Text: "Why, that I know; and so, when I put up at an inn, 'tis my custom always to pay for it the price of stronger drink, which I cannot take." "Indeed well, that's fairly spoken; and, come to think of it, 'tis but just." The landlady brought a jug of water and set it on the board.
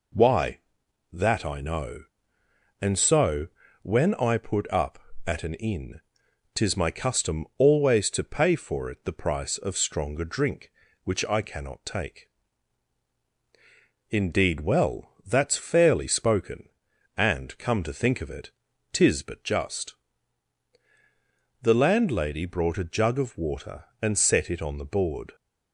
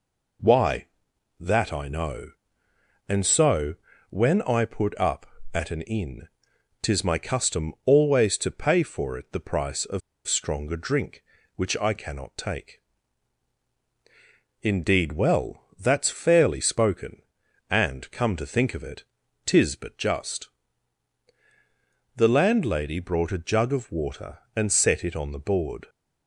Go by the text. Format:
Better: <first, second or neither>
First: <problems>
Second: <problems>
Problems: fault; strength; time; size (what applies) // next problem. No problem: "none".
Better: first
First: none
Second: pauses between "of" and "stronger"; slight; at 10.0 s; 0.26 s long